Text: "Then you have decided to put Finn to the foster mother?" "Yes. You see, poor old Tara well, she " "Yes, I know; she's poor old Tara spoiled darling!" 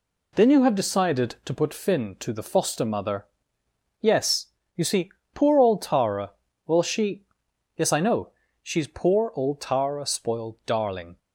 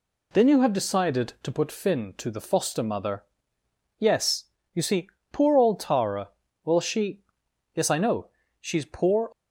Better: first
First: pauses between "Tara" and "well"; slight; at 6.3 s; 0.34 s long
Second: pauses between "Tara" and "well"; slight; at 6.2 s; 0.34 s long // stops before "old Tara spoiled darling"; at 9.3 s

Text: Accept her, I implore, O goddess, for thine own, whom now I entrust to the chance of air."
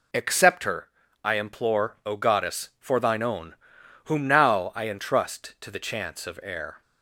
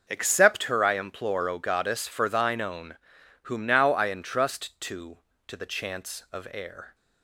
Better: first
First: none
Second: says "to" twice; at 5.4 s

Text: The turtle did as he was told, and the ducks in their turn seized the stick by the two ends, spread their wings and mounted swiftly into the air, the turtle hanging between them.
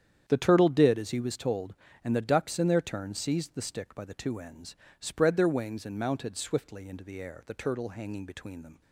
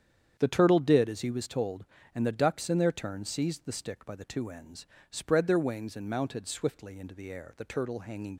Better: first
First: starts louder than the rest; strong; until 1.2 s; 9 dB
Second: starts louder than the rest; strong; until 1.3 s; 8.5 dB // stops before "between them"; at 8.3 s

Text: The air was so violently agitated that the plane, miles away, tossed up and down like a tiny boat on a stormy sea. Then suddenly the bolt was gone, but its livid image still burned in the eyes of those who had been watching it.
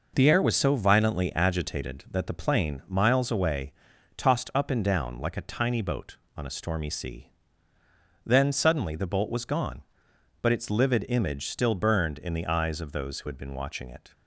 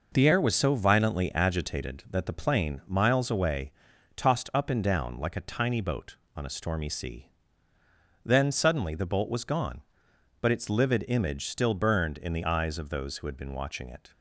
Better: neither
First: none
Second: none

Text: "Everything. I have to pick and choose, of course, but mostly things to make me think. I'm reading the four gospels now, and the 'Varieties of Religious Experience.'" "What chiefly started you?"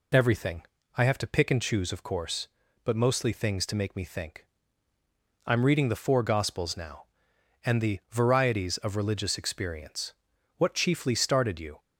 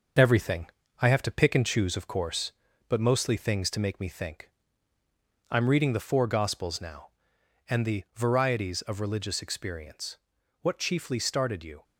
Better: first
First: none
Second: gets quieter; noticeable; throughout; 4.5 dB

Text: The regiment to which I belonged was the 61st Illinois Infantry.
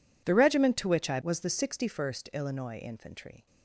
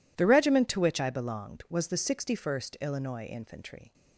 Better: second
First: skips "belonged"; at 1.2 s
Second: none

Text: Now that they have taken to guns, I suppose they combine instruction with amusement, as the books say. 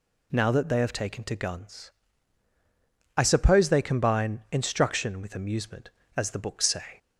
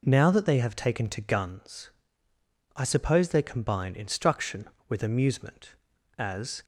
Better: first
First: none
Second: stops before "the books say"; at 6.6 s

